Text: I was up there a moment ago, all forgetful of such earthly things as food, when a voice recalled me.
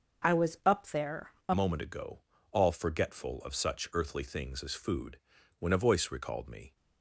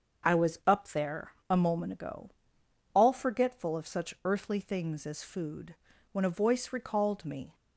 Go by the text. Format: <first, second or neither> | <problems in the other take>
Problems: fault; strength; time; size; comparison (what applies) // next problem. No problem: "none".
second | starts louder than the rest; until 1.5 s; 6.5 dB; also in the second // pauses between "there" and "a"; slight; at 1.3 s; 0.16 s long; slight in the second // changes voice at "moment"; from 1.5 s on; 5.2 s long